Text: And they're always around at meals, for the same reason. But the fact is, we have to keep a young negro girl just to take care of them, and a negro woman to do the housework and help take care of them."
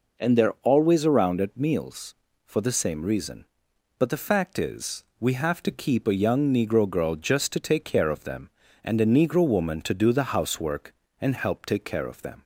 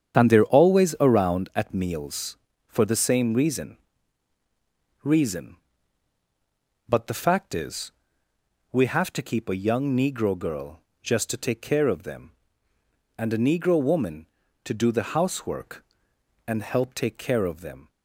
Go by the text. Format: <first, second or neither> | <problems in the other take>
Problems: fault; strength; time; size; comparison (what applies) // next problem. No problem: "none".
first | starts louder than the rest; strong; until 1.1 s; 8 dB // says "reason" twice; at 5.0 s // pauses between "girl" and "just"; slight; at 10.7 s; 0.22 s long